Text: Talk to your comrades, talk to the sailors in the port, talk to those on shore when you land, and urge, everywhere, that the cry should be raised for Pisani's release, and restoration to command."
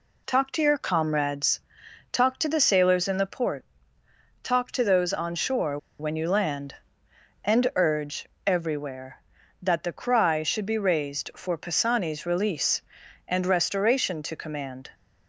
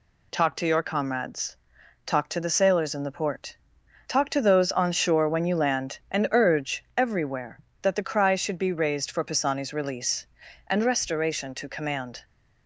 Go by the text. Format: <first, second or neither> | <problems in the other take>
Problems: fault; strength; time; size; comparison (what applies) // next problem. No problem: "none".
second | pauses between "shore" and "when"; slight; at 5.7 s; 0.21 s long